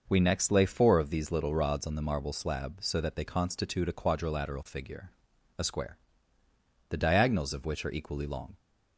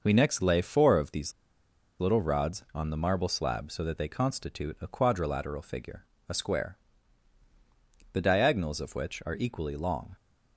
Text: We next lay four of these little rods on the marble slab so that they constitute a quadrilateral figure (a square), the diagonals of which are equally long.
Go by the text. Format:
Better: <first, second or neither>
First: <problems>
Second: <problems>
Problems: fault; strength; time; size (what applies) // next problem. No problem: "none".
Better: first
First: none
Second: pauses between "these" and "little"; noticeable; at 1.3 s; 0.67 s long